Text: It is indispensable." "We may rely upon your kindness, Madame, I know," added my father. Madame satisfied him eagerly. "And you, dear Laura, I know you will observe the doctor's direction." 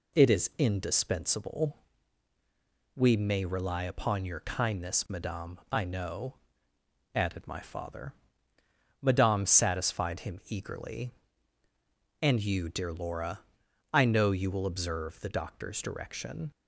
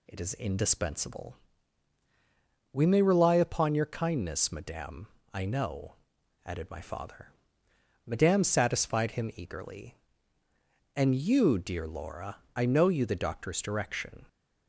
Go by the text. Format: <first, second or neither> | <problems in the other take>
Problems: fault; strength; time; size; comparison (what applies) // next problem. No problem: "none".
first | skips "will observe"; at 13.0 s